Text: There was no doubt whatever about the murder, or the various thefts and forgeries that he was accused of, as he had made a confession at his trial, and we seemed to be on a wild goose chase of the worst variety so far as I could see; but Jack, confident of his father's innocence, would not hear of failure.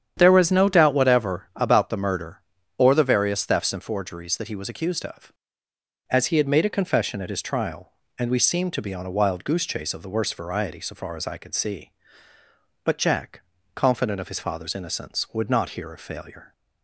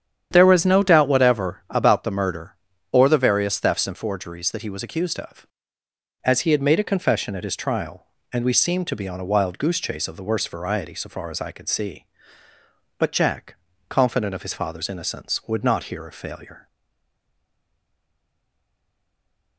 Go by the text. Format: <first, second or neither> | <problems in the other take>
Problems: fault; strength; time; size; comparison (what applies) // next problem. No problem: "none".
first | starts louder than the rest; strong; until 1.3 s; 9 dB; strong in the first // stays silent after the last word; strong; from 16.6 s on; 2.9 s long